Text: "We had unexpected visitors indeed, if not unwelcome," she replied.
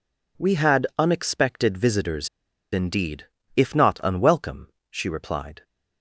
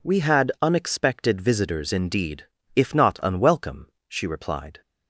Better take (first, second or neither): second